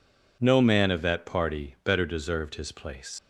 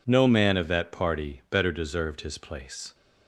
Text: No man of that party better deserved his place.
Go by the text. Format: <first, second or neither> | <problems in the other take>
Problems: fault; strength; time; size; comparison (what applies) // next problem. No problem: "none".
second | leaves "place" unfinished; at 3.1 s; 95 ms